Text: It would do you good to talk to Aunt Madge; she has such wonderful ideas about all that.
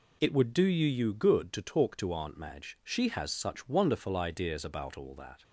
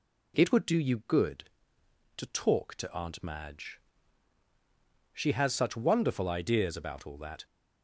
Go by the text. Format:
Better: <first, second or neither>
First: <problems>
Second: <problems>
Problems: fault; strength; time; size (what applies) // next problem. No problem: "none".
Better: second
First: says "you" twice; at 0.8 s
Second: none